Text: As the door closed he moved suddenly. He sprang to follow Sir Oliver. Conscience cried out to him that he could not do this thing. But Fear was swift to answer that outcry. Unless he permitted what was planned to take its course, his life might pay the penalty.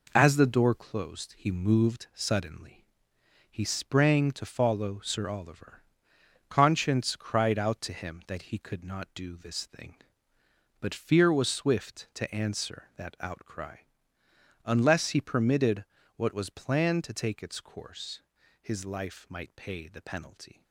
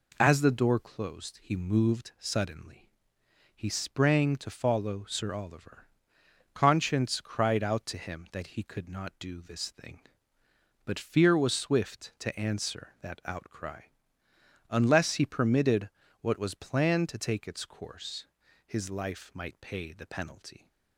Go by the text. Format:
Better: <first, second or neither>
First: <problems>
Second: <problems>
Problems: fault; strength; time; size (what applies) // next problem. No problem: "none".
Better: second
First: gets quieter; throughout; 6.5 dB // pauses between "permitted" and "what"; slight; at 15.8 s; 0.32 s long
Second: pauses between "permitted" and "what"; slight; at 15.8 s; 0.32 s long